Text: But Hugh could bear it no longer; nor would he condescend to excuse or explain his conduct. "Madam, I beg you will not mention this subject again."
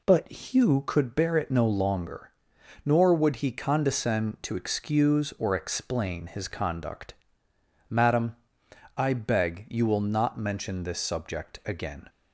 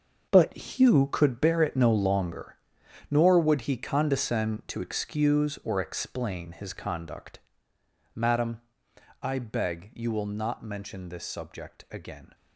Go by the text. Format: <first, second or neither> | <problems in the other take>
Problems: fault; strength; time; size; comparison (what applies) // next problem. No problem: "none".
first | gets quieter; strong; throughout; 12.5 dB